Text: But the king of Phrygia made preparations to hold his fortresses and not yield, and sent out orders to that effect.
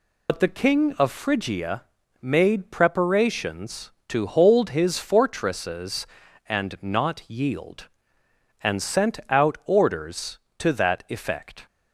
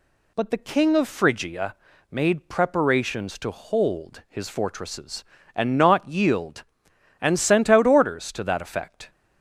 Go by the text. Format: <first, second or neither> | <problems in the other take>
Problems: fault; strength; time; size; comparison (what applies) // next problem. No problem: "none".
second | loses the start of "But"; at 0.2 s; 65 ms // pauses between "Phrygia" and "made"; at 1.8 s; 0.38 s long; slight in the second